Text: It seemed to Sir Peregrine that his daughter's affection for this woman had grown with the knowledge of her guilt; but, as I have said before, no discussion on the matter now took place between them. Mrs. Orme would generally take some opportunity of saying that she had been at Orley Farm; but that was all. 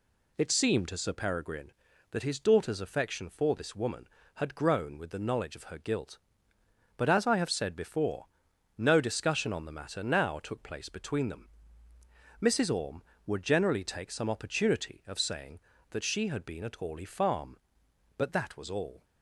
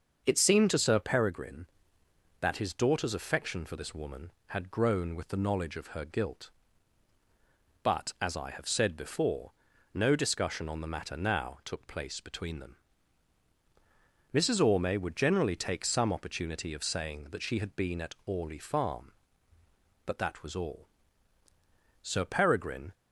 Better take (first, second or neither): first